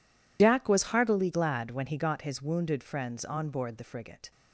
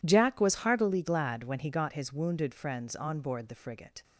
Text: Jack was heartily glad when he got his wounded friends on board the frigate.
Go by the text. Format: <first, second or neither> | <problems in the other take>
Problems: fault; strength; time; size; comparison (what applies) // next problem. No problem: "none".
second | loses the start of "Jack"; at 0.3 s; 90 ms